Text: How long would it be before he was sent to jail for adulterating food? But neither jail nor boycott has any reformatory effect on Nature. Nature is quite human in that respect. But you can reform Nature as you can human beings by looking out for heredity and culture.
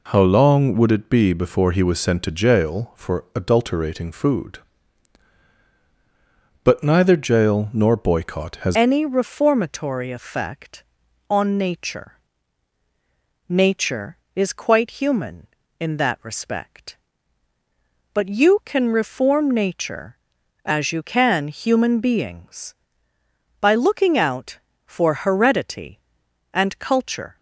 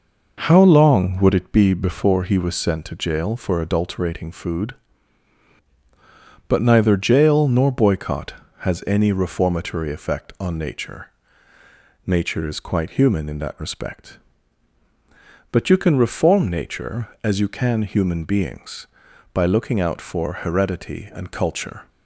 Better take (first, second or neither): second